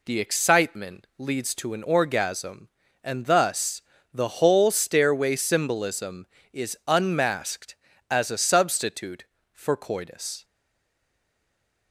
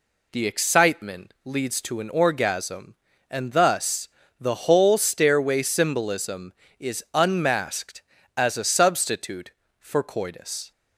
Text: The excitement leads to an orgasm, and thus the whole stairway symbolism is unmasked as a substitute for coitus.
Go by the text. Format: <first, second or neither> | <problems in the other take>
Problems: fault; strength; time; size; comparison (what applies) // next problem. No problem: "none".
second | pauses between "thus" and "the"; slight; at 3.8 s; 0.30 s long; slight in the second // stays silent after the last word; noticeable; from 10.4 s on; 1.5 s long